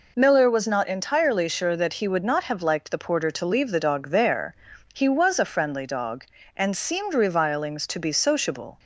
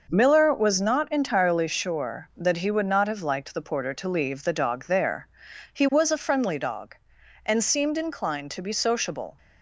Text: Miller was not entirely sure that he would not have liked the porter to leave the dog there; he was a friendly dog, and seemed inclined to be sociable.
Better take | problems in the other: second | says "revilings" for "inclined"; at 7.1 s

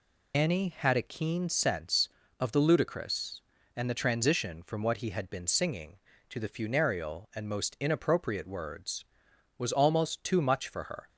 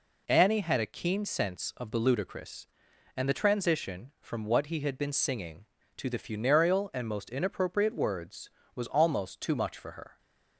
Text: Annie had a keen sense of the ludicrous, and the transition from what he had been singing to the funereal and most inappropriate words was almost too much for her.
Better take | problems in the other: second | loses the start of "Annie"; at 0.3 s; 95 ms

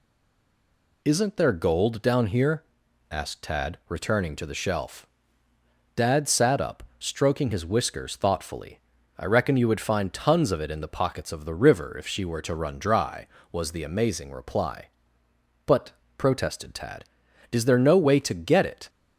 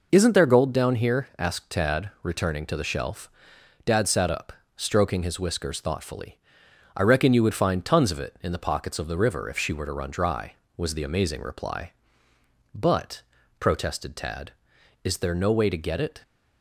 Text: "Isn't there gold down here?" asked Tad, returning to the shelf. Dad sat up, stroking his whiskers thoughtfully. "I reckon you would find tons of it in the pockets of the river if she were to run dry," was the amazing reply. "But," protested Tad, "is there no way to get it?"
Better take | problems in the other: second | stays silent before the first word; until 1.0 s; 1.0 s long

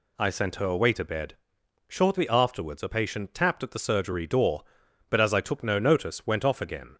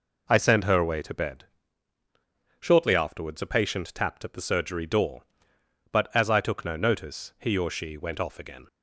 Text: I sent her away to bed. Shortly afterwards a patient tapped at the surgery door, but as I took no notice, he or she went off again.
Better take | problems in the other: second | skips "he or she"; at 6.2 s

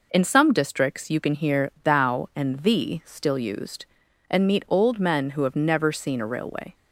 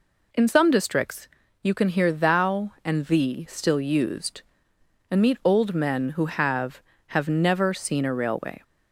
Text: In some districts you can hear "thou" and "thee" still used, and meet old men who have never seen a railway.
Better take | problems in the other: first | pauses between "districts" and "you"; slight; at 1.2 s; 0.34 s long // says "have" twice; at 7.0 s

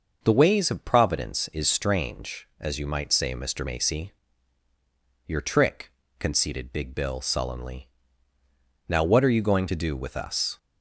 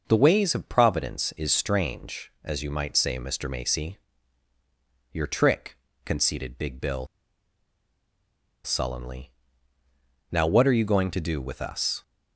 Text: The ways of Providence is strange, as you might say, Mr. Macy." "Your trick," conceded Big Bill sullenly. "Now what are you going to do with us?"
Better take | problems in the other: first | pauses between "Bill" and "sullenly"; strong; at 7.0 s; 1.5 s long

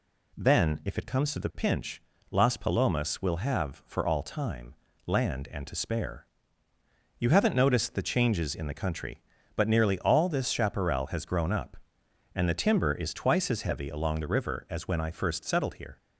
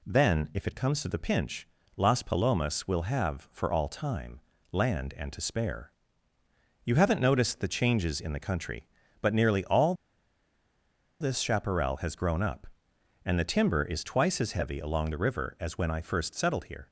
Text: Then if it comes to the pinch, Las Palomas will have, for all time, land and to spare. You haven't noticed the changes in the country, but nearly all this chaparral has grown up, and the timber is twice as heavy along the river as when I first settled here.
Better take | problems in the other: first | pauses between "all" and "this"; strong; at 9.9 s; 1.2 s long

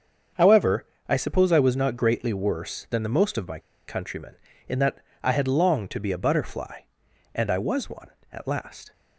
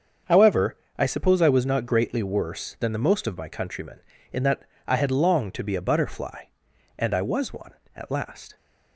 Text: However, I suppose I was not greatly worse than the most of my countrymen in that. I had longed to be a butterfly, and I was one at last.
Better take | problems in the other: second | starts louder than the rest; until 1.5 s; 6.5 dB; also in the second // pauses between "my" and "countrymen"; slight; at 3.5 s; 0.28 s long

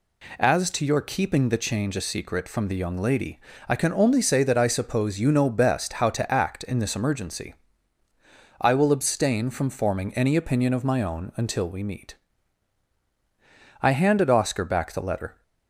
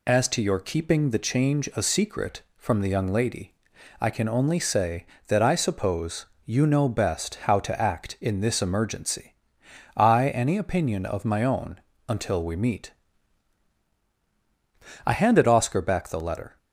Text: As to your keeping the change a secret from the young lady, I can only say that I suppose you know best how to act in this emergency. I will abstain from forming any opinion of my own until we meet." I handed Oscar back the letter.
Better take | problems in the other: first | pauses between "suppose" and "you"; slight; at 6.2 s; 0.20 s long // skips "will abstain from forming"; at 10.2 s // pauses between "own" and "until"; slight; at 11.7 s; 0.30 s long

